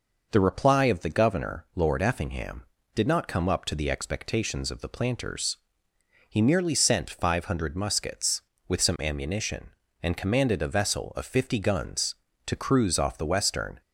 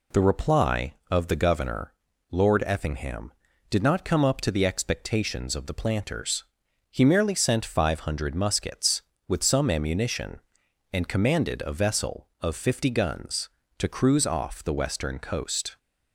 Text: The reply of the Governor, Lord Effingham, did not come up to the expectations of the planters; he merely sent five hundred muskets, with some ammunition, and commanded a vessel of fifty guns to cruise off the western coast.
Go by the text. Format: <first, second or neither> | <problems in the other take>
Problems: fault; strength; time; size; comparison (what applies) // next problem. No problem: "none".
second | stops before "coast"; at 13.8 s